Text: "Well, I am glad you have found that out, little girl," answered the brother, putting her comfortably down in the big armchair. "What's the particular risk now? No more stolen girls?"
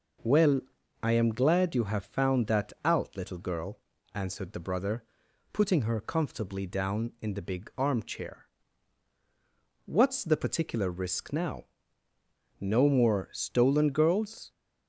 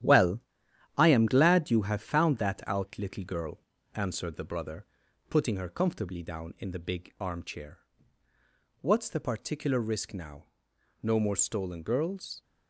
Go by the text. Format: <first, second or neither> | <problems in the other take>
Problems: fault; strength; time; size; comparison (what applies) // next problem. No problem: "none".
first | gets quieter; strong; throughout; 7.5 dB